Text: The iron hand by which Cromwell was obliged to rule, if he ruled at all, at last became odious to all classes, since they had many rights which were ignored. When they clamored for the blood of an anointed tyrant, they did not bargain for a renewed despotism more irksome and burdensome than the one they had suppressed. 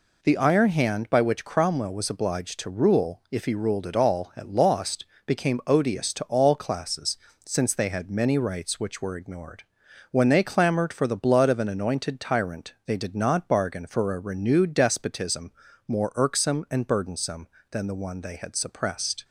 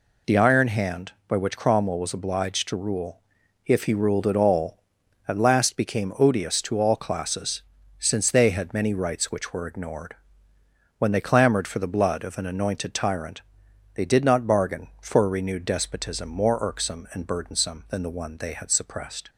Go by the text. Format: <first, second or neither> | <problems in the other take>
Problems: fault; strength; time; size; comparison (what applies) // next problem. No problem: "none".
second | says "lost" for "last"; at 4.4 s // pauses between "despotism" and "more"; slight; at 15.5 s; 0.36 s long